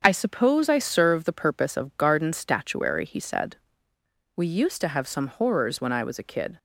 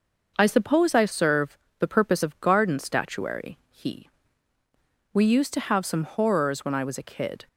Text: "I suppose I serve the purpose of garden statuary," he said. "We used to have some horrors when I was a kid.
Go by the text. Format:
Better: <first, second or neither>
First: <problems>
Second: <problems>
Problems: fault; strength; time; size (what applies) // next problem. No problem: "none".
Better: first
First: starts louder than the rest; until 1.0 s; 7 dB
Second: starts louder than the rest; noticeable; until 1.3 s; 6 dB // pauses between "serve" and "the"; slight; at 1.5 s; 0.20 s long // skips "said"; at 4.5 s